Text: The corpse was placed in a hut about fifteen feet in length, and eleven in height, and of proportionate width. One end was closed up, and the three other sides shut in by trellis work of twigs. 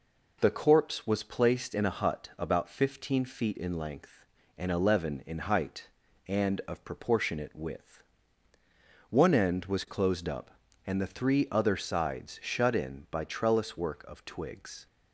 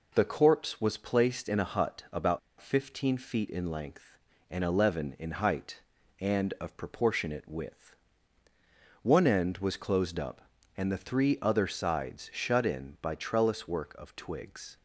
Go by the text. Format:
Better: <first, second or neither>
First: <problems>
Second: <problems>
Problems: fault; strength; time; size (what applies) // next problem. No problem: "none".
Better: first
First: none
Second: pauses between "about" and "fifteen"; slight; at 2.3 s; 0.21 s long